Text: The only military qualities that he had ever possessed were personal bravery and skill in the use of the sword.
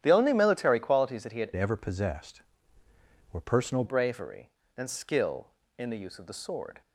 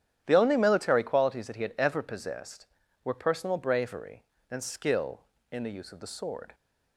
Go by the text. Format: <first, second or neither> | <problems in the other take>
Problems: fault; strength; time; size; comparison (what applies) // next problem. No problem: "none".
second | starts louder than the rest; strong; until 1.0 s; 11 dB; strong in the second // changes voice from "ever" to "personal"; from 1.5 to 3.8 s; 2.3 s long